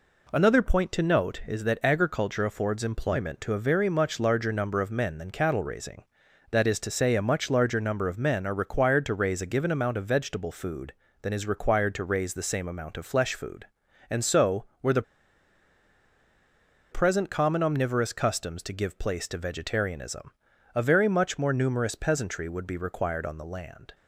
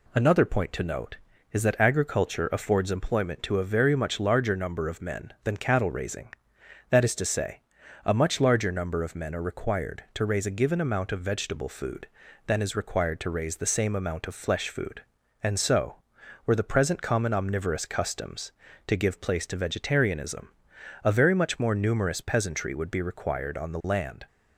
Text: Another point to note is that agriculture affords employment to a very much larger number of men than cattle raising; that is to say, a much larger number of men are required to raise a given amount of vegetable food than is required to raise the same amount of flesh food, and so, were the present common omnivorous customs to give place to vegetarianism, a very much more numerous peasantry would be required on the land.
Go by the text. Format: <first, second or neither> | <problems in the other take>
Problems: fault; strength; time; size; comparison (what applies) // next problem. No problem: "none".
second | pauses between "the" and "present"; strong; at 15.0 s; 1.9 s long